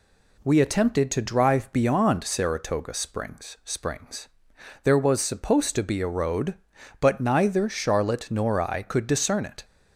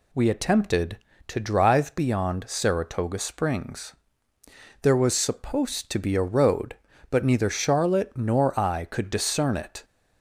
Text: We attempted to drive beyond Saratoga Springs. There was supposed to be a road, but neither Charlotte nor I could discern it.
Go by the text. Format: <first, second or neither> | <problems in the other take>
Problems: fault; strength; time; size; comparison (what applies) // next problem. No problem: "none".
second | says "Springs" twice; at 3.6 s